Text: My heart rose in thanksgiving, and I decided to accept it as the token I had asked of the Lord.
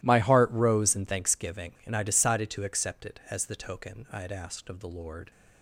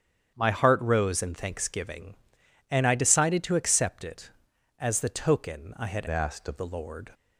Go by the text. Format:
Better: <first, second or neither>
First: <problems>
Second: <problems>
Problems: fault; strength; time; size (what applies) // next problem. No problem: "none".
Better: first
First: none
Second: starts louder than the rest; strong; until 1.3 s; 8.5 dB // changes voice from "asked" to "of"; from 6.0 to 6.5 s; 0.5 s long